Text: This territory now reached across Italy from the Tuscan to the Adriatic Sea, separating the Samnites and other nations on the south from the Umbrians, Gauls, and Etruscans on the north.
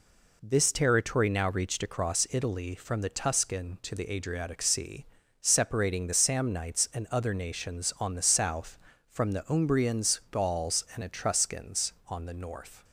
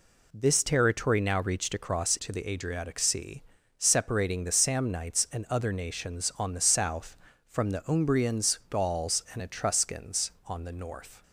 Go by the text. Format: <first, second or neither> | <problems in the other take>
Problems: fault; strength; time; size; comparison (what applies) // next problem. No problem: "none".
first | skips "Italy from the Tuscan"; at 2.1 s